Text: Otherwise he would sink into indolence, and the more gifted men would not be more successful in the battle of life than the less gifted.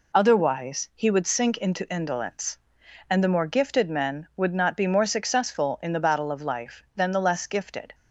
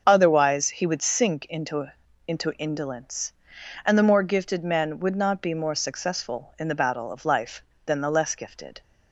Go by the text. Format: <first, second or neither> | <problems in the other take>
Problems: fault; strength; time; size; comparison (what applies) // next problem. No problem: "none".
first | starts louder than the rest; until 1.0 s; 6.5 dB // says "into" twice; at 2.2 s